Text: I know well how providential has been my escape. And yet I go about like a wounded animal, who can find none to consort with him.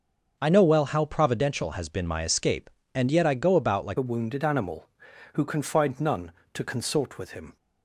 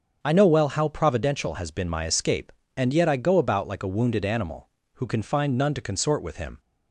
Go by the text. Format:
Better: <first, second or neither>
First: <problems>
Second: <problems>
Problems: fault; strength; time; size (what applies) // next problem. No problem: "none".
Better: second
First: starts louder than the rest; until 1.4 s; 6.5 dB // changes voice at "a"; from 3.9 s on; 3.6 s long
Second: starts louder than the rest; until 1.2 s; 6.5 dB